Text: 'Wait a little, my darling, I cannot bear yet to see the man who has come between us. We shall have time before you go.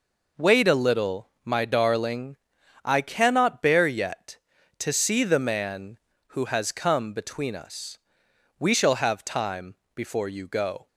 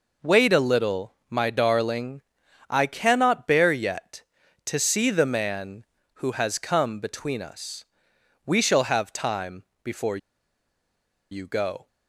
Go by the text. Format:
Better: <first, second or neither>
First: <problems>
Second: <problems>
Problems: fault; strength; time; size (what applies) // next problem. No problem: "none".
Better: first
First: pauses between "time" and "before"; slight; at 9.7 s; 0.18 s long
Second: pauses between "time" and "before"; slight; at 9.6 s; 0.18 s long // pauses between "before" and "you"; at 10.1 s; 1.1 s long